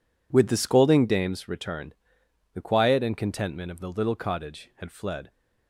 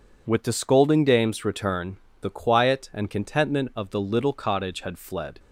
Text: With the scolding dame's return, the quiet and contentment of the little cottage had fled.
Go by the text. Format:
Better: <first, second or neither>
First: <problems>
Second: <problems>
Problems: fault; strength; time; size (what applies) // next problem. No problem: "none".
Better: neither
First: none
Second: none